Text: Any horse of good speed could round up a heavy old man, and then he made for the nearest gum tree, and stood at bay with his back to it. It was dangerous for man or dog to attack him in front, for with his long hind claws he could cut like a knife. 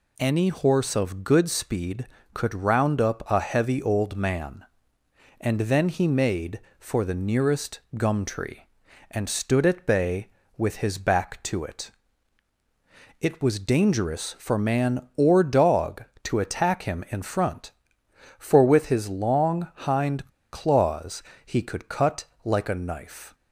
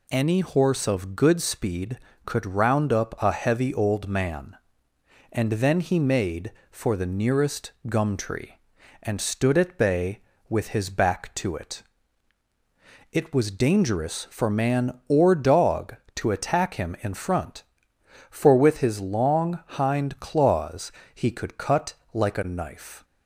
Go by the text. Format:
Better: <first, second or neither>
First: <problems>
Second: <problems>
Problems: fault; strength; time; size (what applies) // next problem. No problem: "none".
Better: second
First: pauses between "nearest" and "gum"; slight; at 7.7 s; 0.18 s long // pauses between "hind" and "claws"; slight; at 20.2 s; 0.23 s long // pauses between "claws" and "he"; slight; at 21.2 s; 0.24 s long // pauses between "cut" and "like"; slight; at 22.2 s; 0.18 s long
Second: pauses between "nearest" and "gum"; slight; at 7.7 s; 0.18 s long // pauses between "claws" and "he"; slight; at 20.8 s; 0.24 s long // pauses between "cut" and "like"; slight; at 21.9 s; 0.18 s long